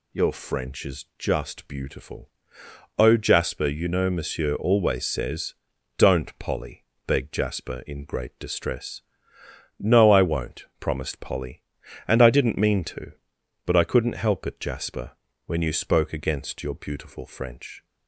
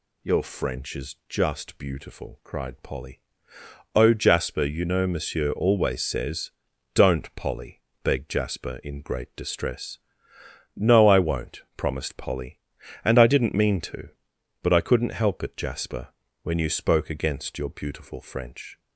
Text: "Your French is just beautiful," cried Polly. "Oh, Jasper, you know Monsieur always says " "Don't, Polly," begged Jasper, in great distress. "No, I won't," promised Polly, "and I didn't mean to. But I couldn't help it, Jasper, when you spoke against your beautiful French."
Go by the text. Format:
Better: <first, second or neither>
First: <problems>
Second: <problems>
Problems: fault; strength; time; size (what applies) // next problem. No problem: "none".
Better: second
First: skips "cried Polly"; at 2.6 s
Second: none